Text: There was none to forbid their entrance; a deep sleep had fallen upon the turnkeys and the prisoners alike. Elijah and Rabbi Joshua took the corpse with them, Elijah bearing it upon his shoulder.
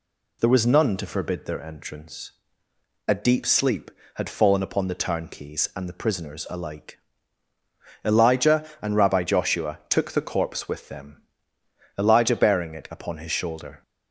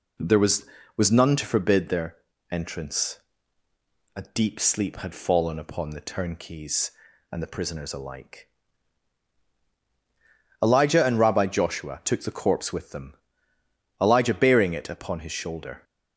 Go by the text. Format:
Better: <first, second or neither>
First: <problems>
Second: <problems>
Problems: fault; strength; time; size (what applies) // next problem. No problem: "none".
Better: first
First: none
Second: says "was" twice; at 0.9 s // pauses between "their" and "entrance"; slight; at 2.1 s; 0.34 s long